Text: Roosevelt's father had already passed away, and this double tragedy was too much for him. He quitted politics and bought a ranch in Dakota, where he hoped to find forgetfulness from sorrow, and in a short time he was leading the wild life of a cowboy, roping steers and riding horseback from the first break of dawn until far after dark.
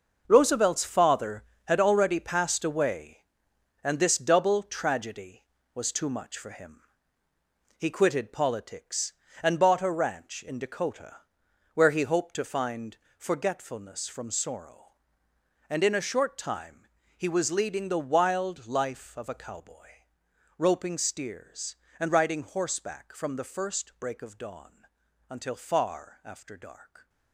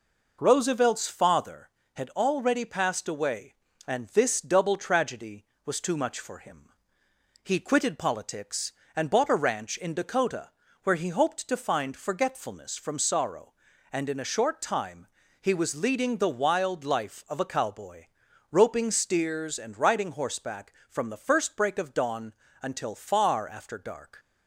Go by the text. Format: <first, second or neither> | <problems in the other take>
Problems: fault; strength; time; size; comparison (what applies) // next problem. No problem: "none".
second | gets quieter; strong; throughout; 11 dB // pauses between "find" and "forgetfulness"; slight; at 12.9 s; 0.22 s long // pauses between "time" and "he"; slight; at 16.8 s; 0.28 s long; slight in the second // pauses between "dawn" and "until"; at 24.8 s; 0.44 s long; slight in the second